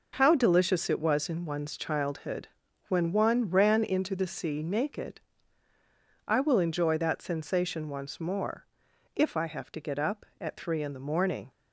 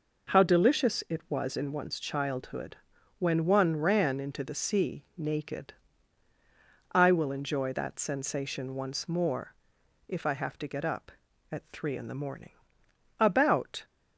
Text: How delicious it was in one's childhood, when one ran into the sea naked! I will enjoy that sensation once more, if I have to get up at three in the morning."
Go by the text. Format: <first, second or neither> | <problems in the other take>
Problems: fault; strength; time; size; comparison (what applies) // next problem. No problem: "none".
first | goes on to say "About"; noticeable; from 13.1 s on; 0.66 s long